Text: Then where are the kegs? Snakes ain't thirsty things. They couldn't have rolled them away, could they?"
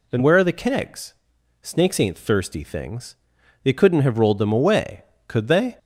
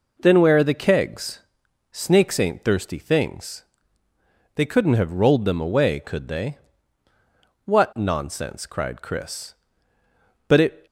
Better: first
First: none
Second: goes on to say "What nonsense cried Chris But it"; strong; from 7.6 s on; 3.2 s long

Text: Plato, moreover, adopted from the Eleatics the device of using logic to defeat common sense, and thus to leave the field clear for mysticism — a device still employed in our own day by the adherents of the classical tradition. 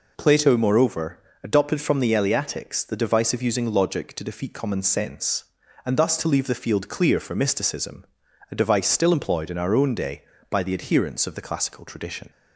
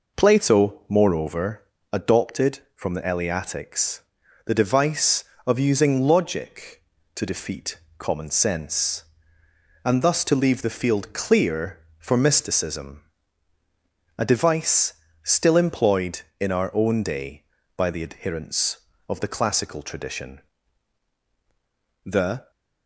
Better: first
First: none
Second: pauses between "Eleatics" and "the"; noticeable; at 3.9 s; 0.46 s long // pauses between "defeat" and "common"; slight; at 7.7 s; 0.20 s long // pauses between "device" and "still"; slight; at 14.9 s; 0.28 s long // goes on to say "The"; slight; from 22.0 s on; 0.46 s long

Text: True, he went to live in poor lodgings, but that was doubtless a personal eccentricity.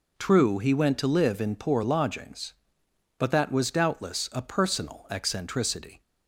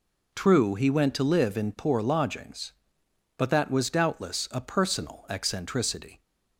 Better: neither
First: none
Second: none

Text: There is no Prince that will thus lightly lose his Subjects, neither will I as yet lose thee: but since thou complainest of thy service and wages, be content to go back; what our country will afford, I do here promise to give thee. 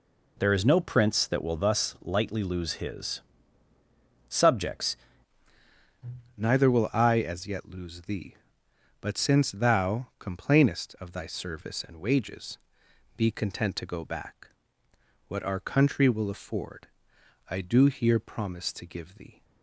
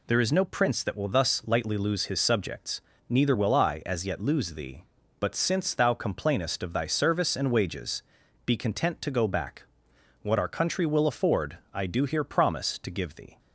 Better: second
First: pauses between "his" and "Subjects"; at 3.2 s; 1.0 s long // changes voice at "neither"; from 6.3 s on; 13.1 s long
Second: none

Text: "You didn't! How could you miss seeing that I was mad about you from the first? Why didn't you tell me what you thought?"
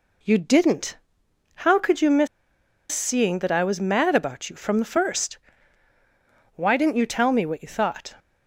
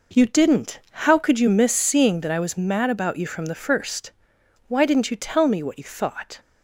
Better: second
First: pauses between "miss" and "seeing"; noticeable; at 2.2 s; 0.64 s long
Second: none

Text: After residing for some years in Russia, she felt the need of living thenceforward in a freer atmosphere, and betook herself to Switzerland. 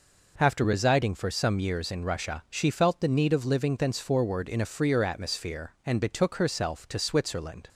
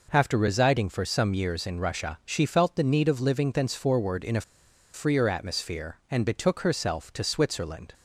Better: first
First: none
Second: pauses between "a" and "freer"; noticeable; at 4.4 s; 0.52 s long

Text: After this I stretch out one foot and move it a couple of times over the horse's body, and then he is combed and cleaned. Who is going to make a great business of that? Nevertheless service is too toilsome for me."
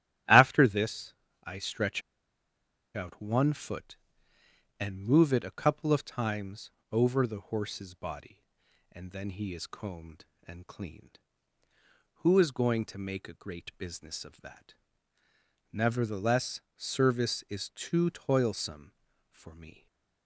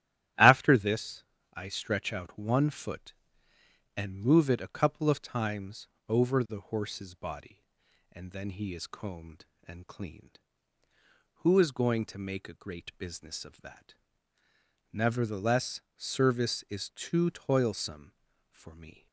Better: second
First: starts louder than the rest; strong; until 1.5 s; 12.5 dB // pauses between "this" and "I"; slight; at 1.1 s; 0.30 s long // pauses between "stretch" and "out"; noticeable; at 2.0 s; 0.93 s long // pauses between "times" and "over"; slight; at 6.7 s; 0.22 s long // pauses between "Nevertheless" and "service"; slight; at 16.6 s; 0.16 s long // stays silent after the last word; slight; from 19.7 s on; 0.5 s long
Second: starts louder than the rest; strong; until 1.6 s; 12.5 dB // pauses between "this" and "I"; slight; at 1.2 s; 0.30 s long // pauses between "times" and "over"; slight; at 5.8 s; 0.22 s long // pauses between "Nevertheless" and "service"; slight; at 15.8 s; 0.16 s long

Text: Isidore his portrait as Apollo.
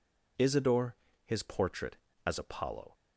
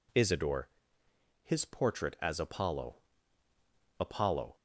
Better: first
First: pauses between "Isidore" and "his"; slight; at 0.9 s; 0.28 s long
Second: pauses between "Isidore" and "his"; noticeable; at 0.6 s; 0.76 s long // says "Apollo" twice; at 3.9 s

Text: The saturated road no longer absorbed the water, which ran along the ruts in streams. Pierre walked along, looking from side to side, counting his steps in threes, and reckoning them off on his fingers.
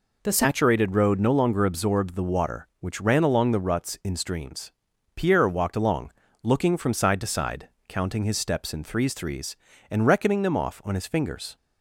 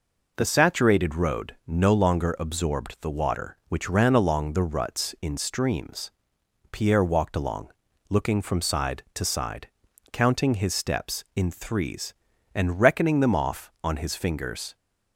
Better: second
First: says "threes" twice; at 9.1 s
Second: none

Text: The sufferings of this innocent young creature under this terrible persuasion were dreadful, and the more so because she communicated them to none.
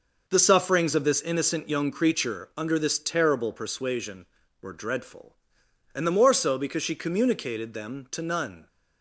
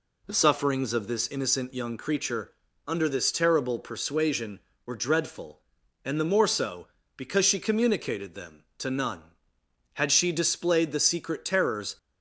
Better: first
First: none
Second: pauses between "creature" and "under"; slight; at 2.5 s; 0.36 s long // goes on to say "Had she displayed the secret terrors"; strong; from 9.9 s on; 2.0 s long

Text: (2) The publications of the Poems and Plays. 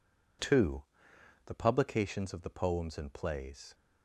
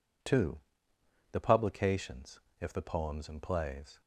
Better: first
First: none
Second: says "if" for "of"; at 2.6 s

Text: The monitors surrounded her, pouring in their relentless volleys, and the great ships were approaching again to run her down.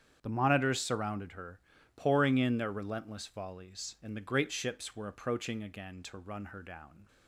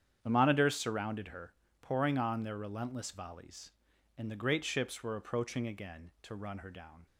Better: first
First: starts louder than the rest; strong; until 1.2 s; 8.5 dB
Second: starts louder than the rest; strong; until 1.2 s; 8.5 dB // says "on" for "in"; at 2.1 s

